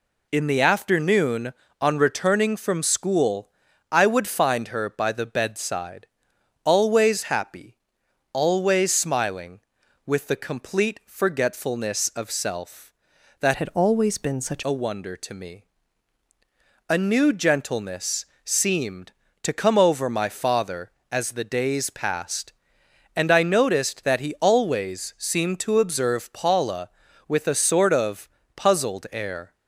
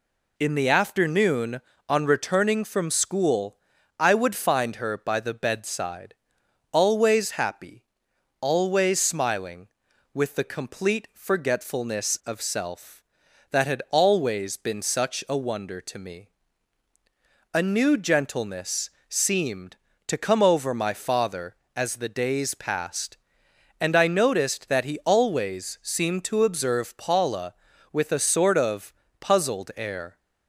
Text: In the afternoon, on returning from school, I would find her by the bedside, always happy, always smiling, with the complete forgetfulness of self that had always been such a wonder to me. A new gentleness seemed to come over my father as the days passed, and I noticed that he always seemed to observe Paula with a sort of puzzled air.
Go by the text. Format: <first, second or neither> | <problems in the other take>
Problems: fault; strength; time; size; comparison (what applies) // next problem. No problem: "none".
second | changes voice from "had" to "such"; from 13.5 to 14.6 s; 1.1 s long // pauses between "gentleness" and "seemed"; slight; at 18.2 s; 0.18 s long; slight in the second // pauses between "of" and "puzzled"; slight; at 28.2 s; 0.26 s long; slight in the second